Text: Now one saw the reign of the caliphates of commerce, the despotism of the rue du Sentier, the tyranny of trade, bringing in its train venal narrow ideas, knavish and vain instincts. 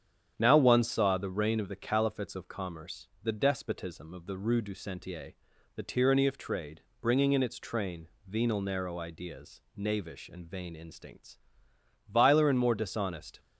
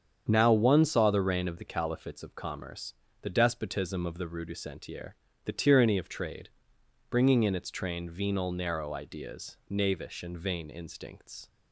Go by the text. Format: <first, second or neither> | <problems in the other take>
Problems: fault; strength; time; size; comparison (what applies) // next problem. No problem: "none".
second | starts louder than the rest; strong; until 1.3 s; 9 dB; strong in the second // pauses between "train" and "venal"; slight; at 8.0 s; 0.18 s long // goes on to say "Viler and more dishonest"; noticeable; from 12.0 s on; 1.3 s long